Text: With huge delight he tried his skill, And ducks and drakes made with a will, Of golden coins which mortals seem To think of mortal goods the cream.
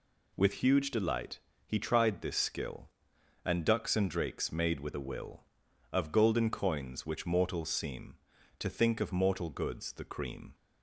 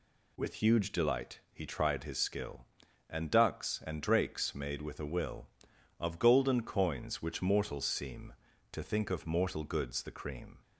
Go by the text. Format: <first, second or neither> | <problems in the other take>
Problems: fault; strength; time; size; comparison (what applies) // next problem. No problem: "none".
second | pauses between "delight" and "he"; slight; at 1.3 s; 0.28 s long // says "this" for "his"; at 2.2 s